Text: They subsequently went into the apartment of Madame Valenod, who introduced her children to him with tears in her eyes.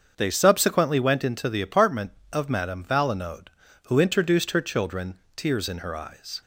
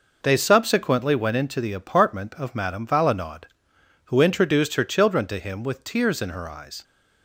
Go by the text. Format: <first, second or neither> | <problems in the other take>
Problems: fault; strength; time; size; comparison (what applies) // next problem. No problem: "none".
second | starts louder than the rest; until 1.1 s; 7 dB // skips "to him with"; at 5.2 s